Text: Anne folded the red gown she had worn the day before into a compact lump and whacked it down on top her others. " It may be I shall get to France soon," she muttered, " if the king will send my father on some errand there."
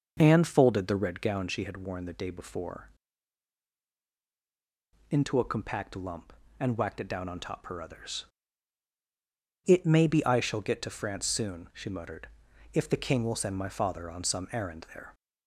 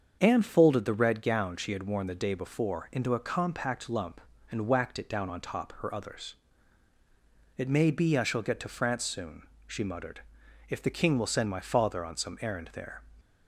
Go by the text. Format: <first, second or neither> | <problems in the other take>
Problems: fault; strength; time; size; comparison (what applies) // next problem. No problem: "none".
second | starts louder than the rest; noticeable; until 1.2 s; 6 dB; also in the second // pauses between "before" and "into"; strong; at 2.8 s; 2.2 s long